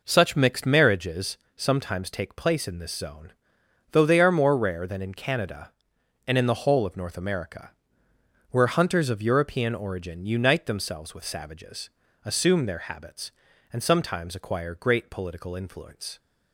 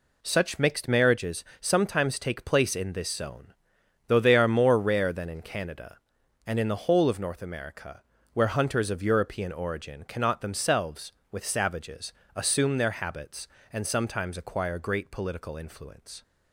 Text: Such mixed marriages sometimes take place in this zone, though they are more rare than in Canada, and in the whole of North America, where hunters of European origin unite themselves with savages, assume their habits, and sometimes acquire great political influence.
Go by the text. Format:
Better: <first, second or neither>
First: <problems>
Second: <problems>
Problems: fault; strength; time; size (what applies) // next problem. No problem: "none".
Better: first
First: pauses between "marriages" and "sometimes"; slight; at 1.3 s; 0.18 s long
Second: pauses between "marriages" and "sometimes"; slight; at 1.4 s; 0.18 s long // says "cannot" for "unite"; at 10.0 s